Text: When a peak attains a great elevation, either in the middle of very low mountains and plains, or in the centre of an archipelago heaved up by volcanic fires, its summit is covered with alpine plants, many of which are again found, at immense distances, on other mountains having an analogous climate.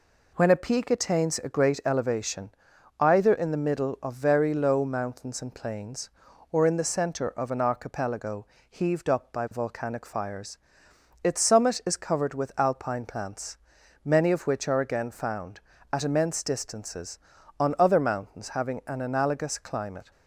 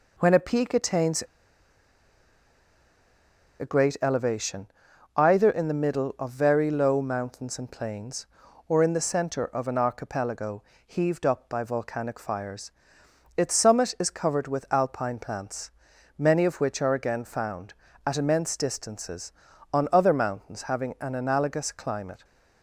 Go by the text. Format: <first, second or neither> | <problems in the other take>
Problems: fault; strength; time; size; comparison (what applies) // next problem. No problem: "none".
first | pauses between "attains" and "a"; strong; at 1.2 s; 2.3 s long // pauses between "archipelago" and "heaved"; slight; at 10.6 s; 0.20 s long; slight in the first